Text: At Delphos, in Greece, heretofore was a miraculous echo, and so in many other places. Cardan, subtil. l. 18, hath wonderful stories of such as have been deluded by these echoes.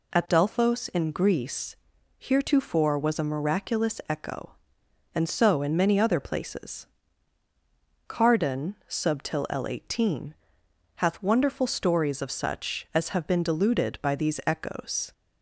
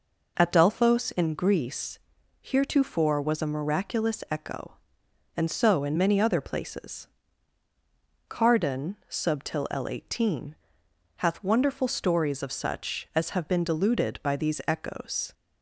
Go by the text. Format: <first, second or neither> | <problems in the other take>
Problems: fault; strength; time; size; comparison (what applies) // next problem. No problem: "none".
first | starts louder than the rest; noticeable; until 1.3 s; 5 dB